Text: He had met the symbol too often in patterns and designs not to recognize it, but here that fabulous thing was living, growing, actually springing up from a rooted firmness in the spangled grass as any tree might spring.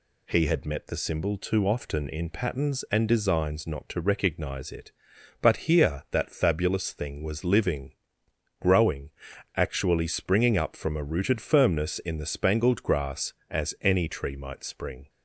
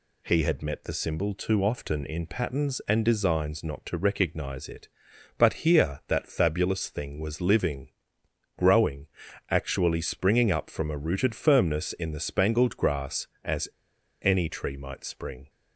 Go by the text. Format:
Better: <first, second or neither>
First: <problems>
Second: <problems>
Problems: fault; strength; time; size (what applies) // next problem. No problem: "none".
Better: first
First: none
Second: pauses between "as" and "any"; noticeable; at 13.6 s; 0.52 s long